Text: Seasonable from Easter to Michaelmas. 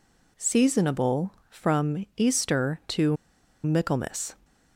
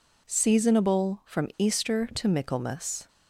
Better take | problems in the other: second | pauses between "to" and "Michaelmas"; noticeable; at 3.1 s; 0.47 s long

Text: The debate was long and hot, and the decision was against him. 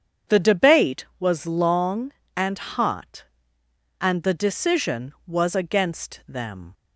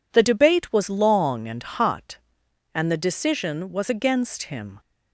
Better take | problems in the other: second | starts louder than the rest; strong; until 1.4 s; 7.5 dB // says "them" for "him"; at 6.2 s

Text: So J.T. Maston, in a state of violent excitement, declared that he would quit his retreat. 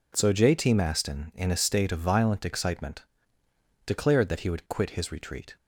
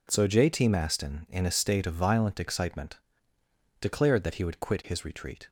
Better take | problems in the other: neither | none

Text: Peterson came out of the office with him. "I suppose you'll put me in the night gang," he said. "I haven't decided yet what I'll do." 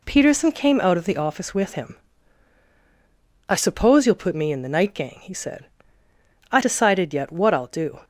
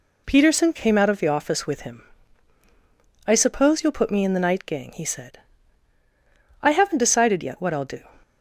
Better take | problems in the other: second | skips "haven't"; at 6.5 s

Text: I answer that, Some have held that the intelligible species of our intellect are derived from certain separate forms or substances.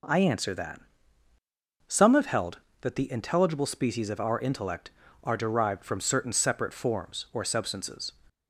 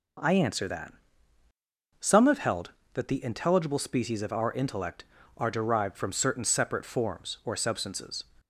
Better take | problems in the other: neither | none

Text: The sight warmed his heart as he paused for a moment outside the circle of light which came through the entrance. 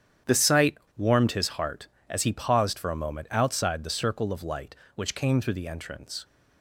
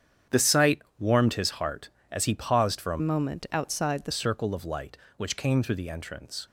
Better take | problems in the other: first | starts louder than the rest; strong; until 1.4 s; 9 dB; strong in the first // pauses between "sight" and "warmed"; slight; at 0.8 s; 0.16 s long; slight in the first // changes voice from "moment" to "the"; from 2.9 to 4.1 s; 1.2 s long

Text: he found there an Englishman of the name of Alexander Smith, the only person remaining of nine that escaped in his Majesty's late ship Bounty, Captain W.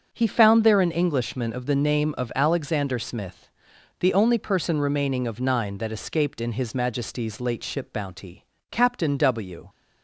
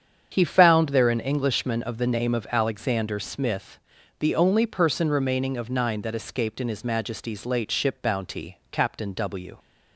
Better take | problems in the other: neither | starts louder than the rest; the same in both

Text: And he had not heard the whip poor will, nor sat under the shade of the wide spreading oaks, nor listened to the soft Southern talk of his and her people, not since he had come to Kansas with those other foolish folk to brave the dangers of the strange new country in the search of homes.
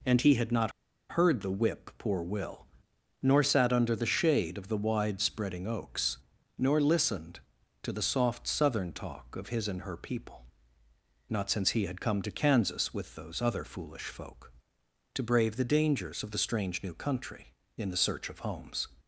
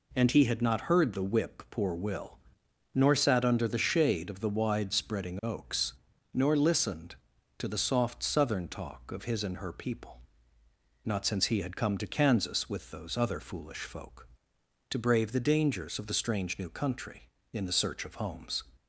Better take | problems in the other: second | pauses between "not" and "heard"; at 0.7 s; 0.38 s long

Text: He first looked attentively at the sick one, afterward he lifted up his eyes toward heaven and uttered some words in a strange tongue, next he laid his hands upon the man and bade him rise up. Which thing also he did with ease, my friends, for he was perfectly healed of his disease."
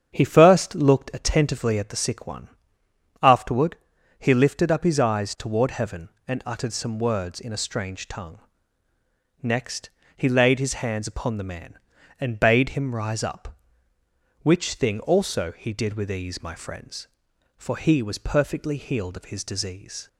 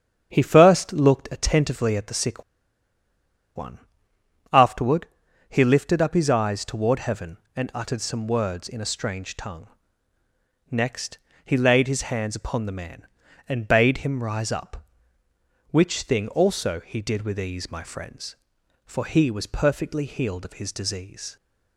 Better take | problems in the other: first | starts louder than the rest; strong; until 1.3 s; 8 dB; strong in the first // pauses between "sick" and "one"; at 2.4 s; 1.1 s long // pauses between "afterward" and "he"; at 5.0 s; 0.42 s long; also in the first // pauses between "next" and "he"; slight; at 11.1 s; 0.26 s long; slight in the first

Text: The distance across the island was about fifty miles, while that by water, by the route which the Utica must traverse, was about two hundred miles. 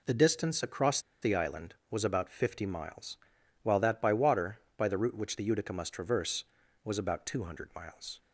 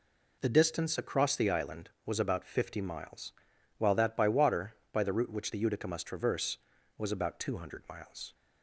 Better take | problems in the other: second | pauses between "across" and "the"; slight; at 0.9 s; 0.23 s long

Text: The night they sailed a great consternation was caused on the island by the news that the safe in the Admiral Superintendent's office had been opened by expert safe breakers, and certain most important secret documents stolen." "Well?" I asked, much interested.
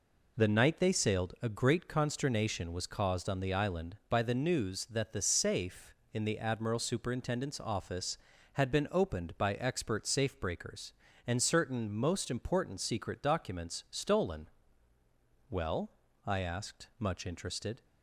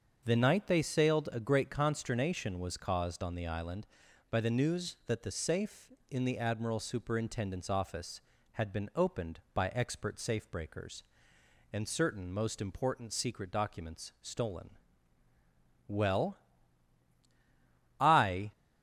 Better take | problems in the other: first | starts louder than the rest; until 1.2 s; 7 dB // stops before "asked much interested"; at 18.5 s

